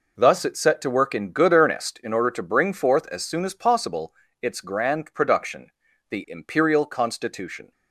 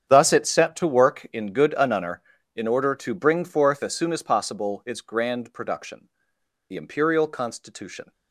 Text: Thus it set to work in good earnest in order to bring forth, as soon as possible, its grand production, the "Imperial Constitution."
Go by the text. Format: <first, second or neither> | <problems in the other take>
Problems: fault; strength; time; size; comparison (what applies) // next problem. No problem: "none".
first | starts louder than the rest; strong; until 1.1 s; 8.5 dB // says "anunner" for "earnest"; at 1.7 s